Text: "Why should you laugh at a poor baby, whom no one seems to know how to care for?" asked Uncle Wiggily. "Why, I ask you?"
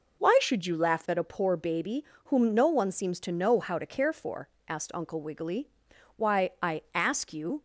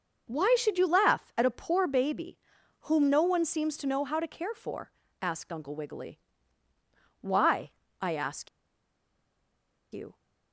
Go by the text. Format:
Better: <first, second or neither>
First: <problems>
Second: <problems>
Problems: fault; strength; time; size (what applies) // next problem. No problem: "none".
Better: first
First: none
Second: starts louder than the rest; noticeable; until 1.3 s; 6 dB // pauses between "ask" and "you"; strong; at 8.4 s; 1.4 s long